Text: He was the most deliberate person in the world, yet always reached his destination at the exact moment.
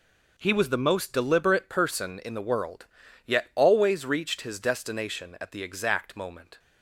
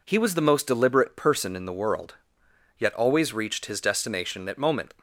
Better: first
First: none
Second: skips "the exact"; at 4.5 s

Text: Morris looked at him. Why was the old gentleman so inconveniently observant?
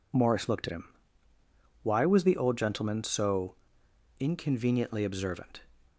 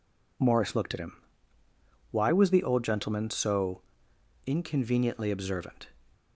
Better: neither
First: pauses between "so" and "inconveniently"; noticeable; at 3.5 s; 0.64 s long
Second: pauses between "so" and "inconveniently"; noticeable; at 3.8 s; 0.64 s long

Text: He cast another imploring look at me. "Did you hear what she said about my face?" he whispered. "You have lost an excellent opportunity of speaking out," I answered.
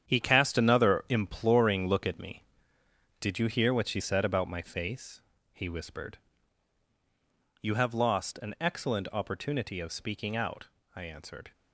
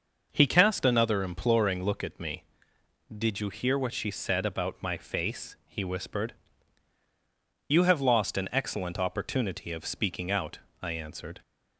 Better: second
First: gets quieter; strong; throughout; 9 dB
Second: none

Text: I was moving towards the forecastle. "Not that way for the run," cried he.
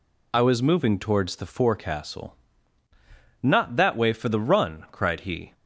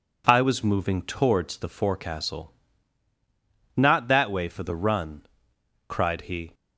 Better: neither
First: none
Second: none

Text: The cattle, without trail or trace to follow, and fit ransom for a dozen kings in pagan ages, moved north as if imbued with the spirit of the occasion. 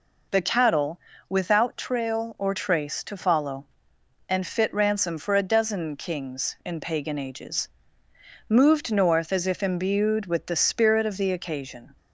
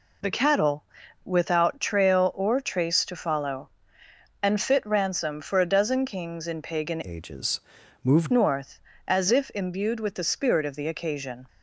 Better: first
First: none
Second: changes voice from "ages" to "moved"; from 7.0 to 8.3 s; 1.3 s long

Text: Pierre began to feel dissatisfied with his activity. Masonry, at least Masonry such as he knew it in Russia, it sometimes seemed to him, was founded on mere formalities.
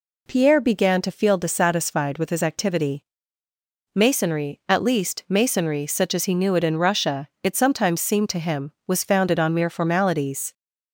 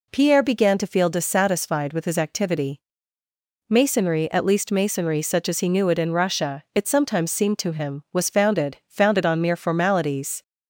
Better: first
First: none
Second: says "founded" twice; at 8.8 s

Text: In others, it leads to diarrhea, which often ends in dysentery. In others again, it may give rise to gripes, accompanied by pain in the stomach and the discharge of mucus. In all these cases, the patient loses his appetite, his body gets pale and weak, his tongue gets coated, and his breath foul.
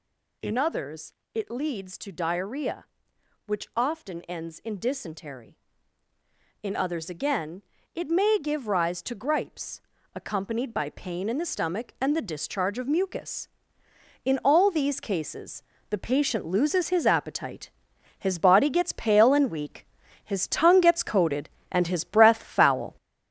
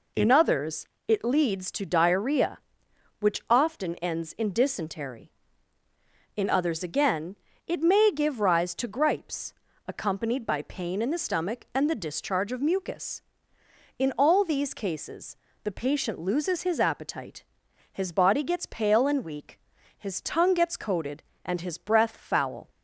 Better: second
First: gets louder; noticeable; throughout; 5.5 dB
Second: none

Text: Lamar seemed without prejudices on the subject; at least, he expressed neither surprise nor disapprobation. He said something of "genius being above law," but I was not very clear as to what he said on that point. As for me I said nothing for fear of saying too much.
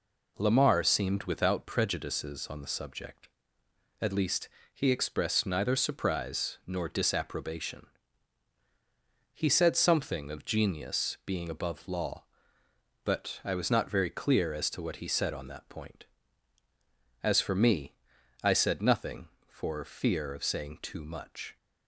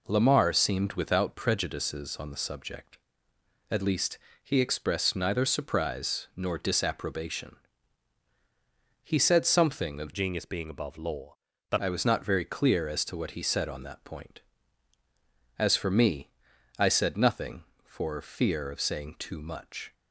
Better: first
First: pauses between "me" and "I"; noticeable; at 17.9 s; 0.48 s long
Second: changes voice from "genius" to "but"; from 10.1 to 11.7 s; 1.6 s long // pauses between "me" and "I"; noticeable; at 16.2 s; 0.48 s long

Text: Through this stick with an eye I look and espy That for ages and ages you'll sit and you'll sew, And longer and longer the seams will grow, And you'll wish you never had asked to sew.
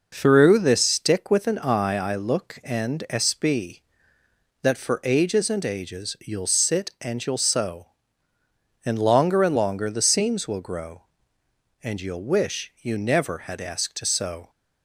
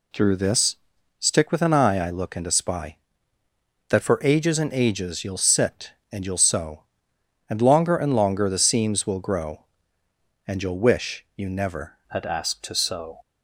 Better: first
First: none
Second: pauses between "this" and "stick"; at 0.7 s; 0.42 s long // changes voice at "had"; from 12.0 s on; 1.1 s long

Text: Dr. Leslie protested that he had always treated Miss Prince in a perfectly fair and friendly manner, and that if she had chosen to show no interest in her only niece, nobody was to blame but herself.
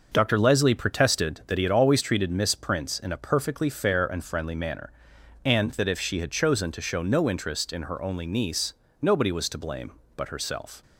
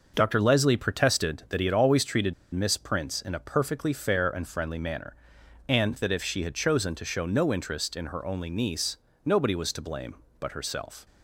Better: first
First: starts louder than the rest; noticeable; until 1.1 s; 6 dB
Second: starts louder than the rest; noticeable; until 1.1 s; 6 dB // pauses between "treated" and "Miss"; slight; at 2.3 s; 0.19 s long

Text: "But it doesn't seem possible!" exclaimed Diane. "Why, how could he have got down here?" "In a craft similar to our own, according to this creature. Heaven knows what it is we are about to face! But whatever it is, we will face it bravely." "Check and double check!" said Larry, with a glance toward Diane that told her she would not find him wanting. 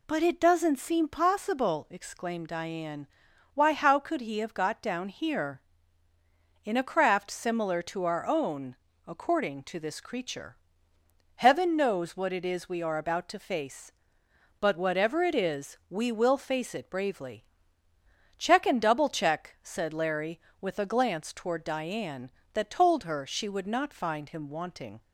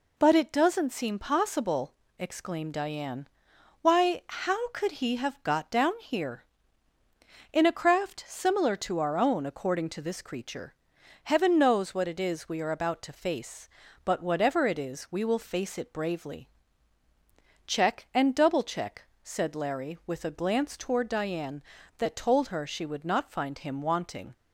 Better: neither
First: none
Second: none

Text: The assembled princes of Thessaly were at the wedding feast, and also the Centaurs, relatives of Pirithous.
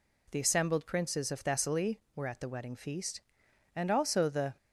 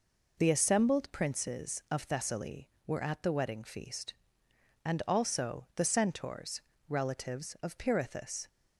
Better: second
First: stops before "Centaurs relatives of Pirithous"; at 4.5 s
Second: none

